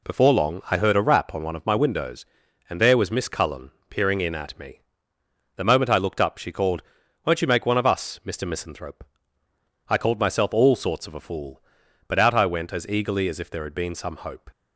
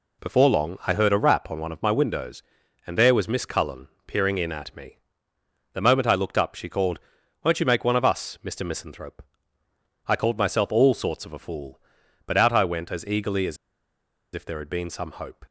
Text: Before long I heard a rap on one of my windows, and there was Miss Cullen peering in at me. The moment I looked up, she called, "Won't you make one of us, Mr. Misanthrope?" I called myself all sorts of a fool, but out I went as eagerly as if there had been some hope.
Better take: first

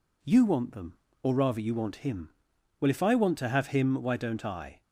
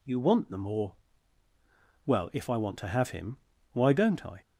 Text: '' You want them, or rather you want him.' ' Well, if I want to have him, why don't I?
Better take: first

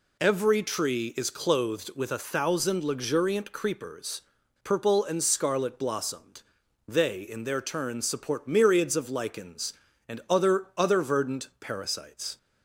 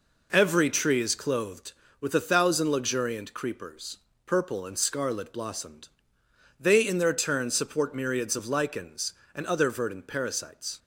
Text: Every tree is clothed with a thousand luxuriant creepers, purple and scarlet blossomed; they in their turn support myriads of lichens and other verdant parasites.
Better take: second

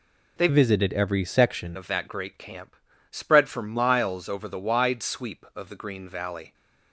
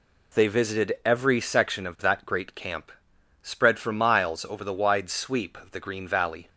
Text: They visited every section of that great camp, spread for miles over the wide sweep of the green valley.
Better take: second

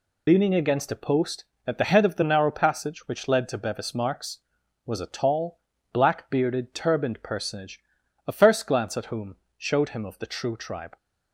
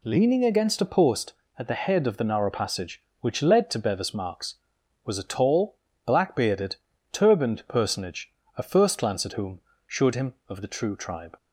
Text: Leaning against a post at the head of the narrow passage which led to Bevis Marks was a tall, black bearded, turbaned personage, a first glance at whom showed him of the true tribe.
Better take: second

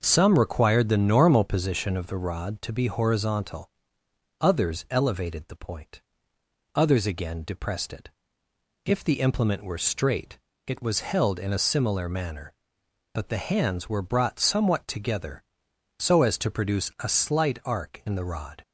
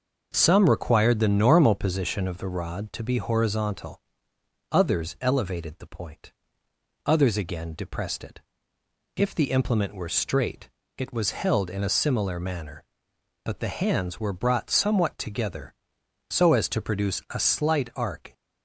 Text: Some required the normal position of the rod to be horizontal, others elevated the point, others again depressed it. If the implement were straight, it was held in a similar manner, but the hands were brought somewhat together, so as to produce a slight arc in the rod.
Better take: first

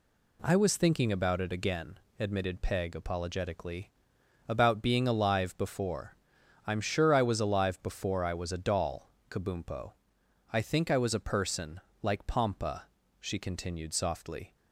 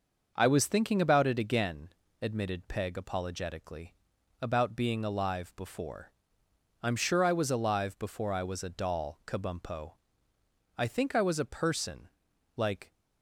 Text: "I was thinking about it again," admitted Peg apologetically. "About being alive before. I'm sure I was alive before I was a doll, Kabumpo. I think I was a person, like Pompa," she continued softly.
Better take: first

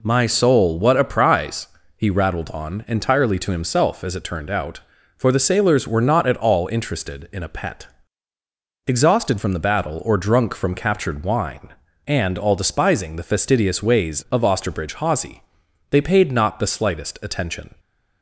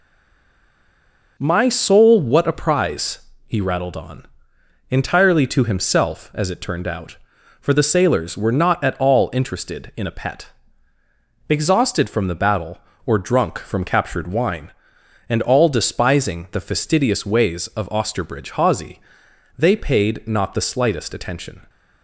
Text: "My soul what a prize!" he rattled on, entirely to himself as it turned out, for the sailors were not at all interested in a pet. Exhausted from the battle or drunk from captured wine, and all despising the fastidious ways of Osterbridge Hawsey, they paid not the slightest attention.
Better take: first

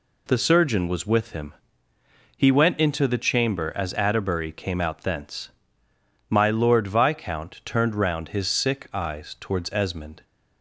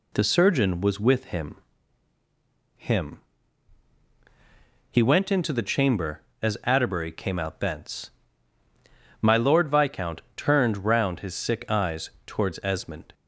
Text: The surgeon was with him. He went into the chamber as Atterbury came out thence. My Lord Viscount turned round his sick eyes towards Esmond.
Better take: first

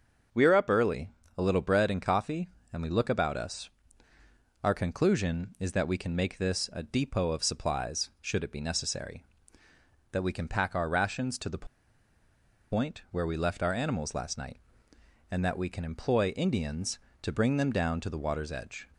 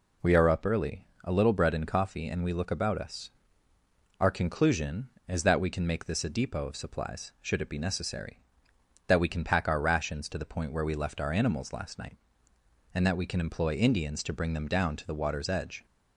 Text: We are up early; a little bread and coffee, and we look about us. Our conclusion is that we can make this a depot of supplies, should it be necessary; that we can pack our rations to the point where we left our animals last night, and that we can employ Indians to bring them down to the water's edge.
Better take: second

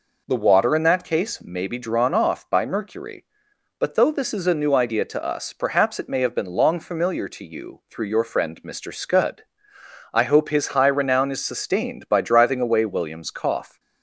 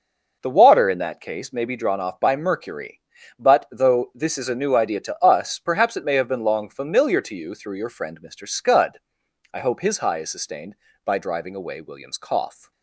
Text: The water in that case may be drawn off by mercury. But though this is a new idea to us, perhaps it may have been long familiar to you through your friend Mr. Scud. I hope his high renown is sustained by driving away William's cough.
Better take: first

